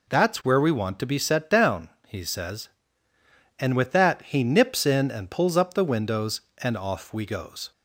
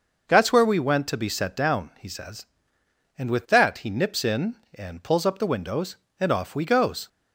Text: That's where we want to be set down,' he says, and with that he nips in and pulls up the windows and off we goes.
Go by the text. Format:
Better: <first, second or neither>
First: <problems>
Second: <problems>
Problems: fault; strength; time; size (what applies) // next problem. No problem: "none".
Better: first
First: none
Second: says "went" for "want"; at 0.7 s